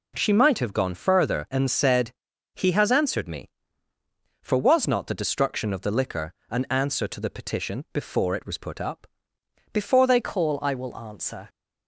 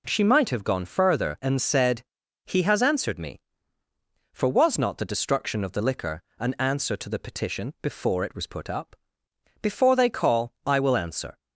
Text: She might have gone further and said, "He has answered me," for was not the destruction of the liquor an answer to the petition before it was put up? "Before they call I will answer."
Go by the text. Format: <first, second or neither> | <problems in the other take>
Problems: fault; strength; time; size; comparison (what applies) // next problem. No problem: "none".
second | pauses between "liquor" and "an"; slight; at 6.3 s; 0.18 s long; slight in the second // changes voice at "call"; from 10.2 s on; 1.2 s long